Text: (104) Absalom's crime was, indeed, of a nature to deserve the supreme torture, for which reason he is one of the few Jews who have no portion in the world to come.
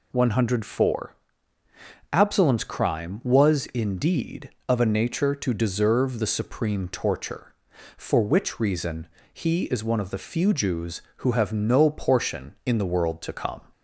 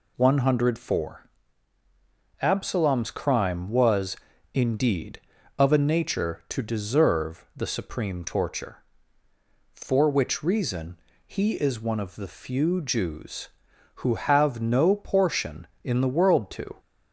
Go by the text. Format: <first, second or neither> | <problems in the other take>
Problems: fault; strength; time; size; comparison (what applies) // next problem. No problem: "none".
first | pauses between "reason" and "he"; slight; at 10.9 s; 0.28 s long; slight in the first // stops before "come"; at 16.7 s